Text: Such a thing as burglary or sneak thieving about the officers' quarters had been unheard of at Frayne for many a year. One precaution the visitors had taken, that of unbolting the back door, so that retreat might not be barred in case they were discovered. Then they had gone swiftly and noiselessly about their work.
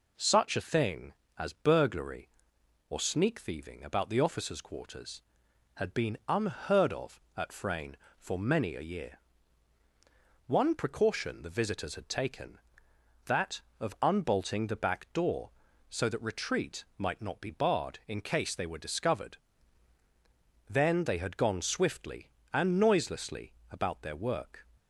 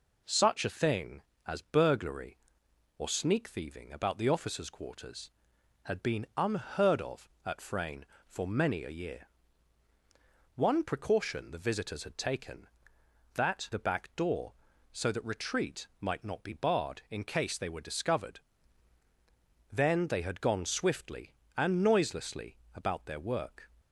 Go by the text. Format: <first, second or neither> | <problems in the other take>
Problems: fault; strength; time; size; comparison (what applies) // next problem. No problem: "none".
first | skips "of unbolting"; at 13.7 s // pauses between "noiselessly" and "about"; slight; at 22.5 s; 0.20 s long; slight in the first